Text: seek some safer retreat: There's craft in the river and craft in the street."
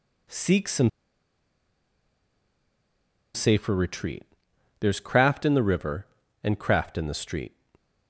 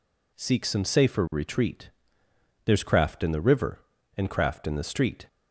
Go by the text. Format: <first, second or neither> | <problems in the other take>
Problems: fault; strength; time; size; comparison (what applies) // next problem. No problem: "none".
second | pauses between "some" and "safer"; strong; at 0.8 s; 2.4 s long